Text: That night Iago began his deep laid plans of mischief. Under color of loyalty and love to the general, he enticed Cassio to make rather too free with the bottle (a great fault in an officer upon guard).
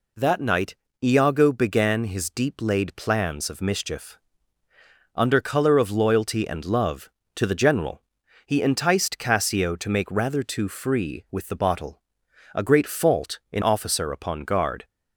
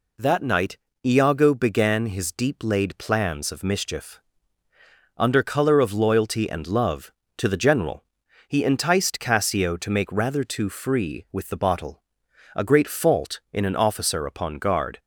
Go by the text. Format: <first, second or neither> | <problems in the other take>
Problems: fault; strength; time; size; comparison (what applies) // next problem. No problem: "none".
second | pauses between "night" and "Iago"; slight; at 0.7 s; 0.26 s long; slight in the second // skips "an"; at 13.6 s